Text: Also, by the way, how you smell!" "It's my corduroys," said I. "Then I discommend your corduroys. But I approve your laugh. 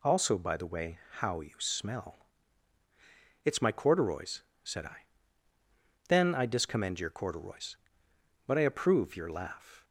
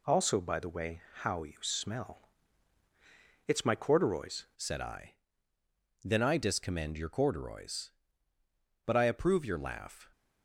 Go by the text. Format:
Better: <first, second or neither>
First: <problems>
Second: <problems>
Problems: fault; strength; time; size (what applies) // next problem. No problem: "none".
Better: first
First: none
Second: changes voice at "said"; from 4.5 s on; 5.5 s long